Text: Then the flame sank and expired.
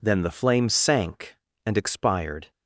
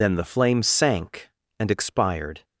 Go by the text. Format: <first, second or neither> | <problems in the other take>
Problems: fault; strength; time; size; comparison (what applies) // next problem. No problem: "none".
first | loses the start of "Then"; at 0.0 s; 50 ms